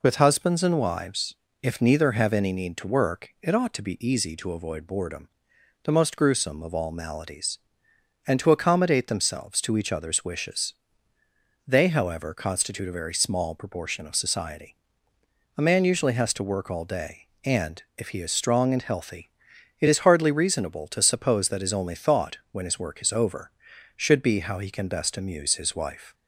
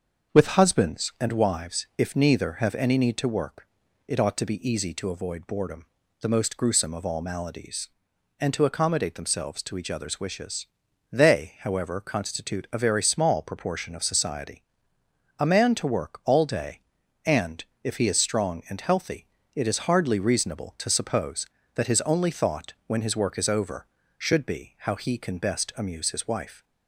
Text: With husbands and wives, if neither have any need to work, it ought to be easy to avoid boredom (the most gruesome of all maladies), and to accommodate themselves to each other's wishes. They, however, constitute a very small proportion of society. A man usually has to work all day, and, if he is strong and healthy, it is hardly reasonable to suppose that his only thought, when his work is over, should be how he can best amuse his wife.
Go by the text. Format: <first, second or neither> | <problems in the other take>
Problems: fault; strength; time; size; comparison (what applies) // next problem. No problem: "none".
first | starts louder than the rest; until 1.3 s; 6.5 dB // skips "usually has"; at 15.7 s